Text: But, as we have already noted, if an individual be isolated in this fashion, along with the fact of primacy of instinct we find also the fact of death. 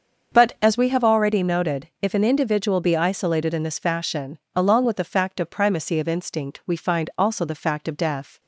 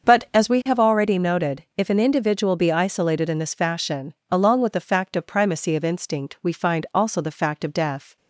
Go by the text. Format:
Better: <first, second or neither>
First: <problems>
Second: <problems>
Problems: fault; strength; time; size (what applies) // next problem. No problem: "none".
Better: neither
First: starts louder than the rest; until 1.4 s; 6.5 dB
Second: starts louder than the rest; until 1.1 s; 6.5 dB